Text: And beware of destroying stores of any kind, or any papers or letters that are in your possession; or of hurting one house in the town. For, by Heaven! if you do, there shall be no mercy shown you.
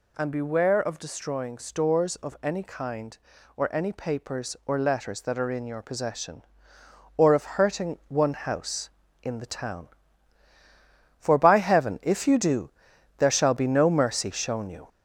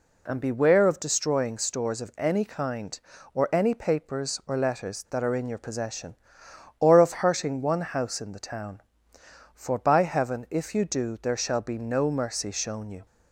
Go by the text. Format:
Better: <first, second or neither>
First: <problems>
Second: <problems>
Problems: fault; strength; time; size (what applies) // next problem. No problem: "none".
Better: second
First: gets louder; noticeable; throughout; 4.5 dB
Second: none